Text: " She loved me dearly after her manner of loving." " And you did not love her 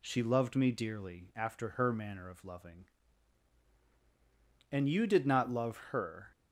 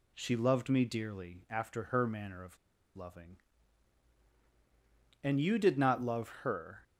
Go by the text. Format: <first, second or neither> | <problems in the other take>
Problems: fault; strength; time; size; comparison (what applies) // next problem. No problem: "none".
first | pauses between "of" and "loving"; at 2.5 s; 0.38 s long // pauses between "love" and "her"; slight; at 6.2 s; 0.16 s long; slight in the first